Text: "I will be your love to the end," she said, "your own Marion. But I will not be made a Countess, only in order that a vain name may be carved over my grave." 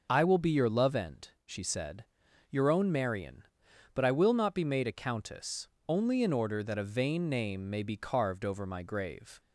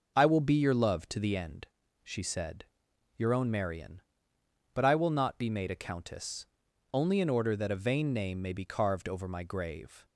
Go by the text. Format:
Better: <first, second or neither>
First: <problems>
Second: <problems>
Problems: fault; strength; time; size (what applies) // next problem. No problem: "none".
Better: second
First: starts louder than the rest; until 1.1 s; 6 dB // skips "to the"; at 0.9 s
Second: none